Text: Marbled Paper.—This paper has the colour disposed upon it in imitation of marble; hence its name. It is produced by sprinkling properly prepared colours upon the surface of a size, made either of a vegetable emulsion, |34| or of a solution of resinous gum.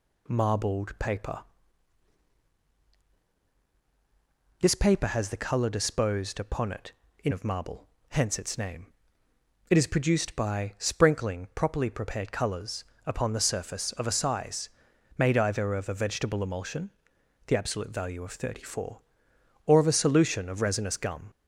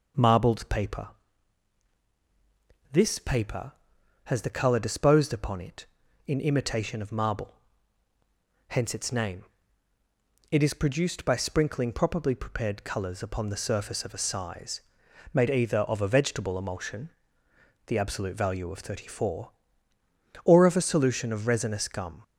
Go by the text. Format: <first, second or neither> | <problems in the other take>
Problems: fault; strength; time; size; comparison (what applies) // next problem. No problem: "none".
second | skips "imitation"; at 7.3 s // pauses between "colours" and "upon"; slight; at 12.8 s; 0.22 s long